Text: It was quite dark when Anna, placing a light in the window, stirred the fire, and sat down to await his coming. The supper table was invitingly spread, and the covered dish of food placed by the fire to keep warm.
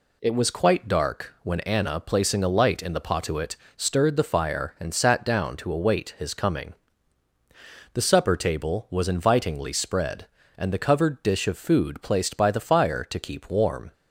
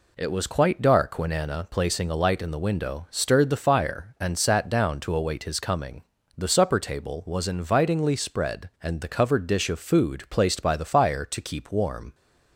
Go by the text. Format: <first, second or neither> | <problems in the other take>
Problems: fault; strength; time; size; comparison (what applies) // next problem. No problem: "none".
second | says "potuit" for "window"; at 3.0 s